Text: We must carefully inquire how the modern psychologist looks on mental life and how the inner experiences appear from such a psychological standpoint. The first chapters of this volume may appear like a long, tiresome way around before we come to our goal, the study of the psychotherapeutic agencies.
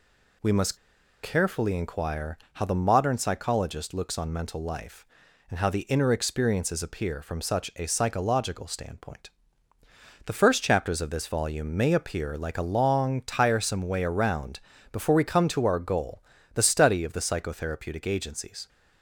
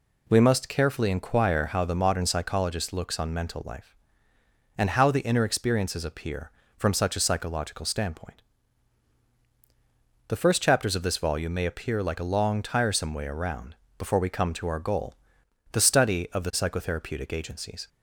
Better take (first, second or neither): second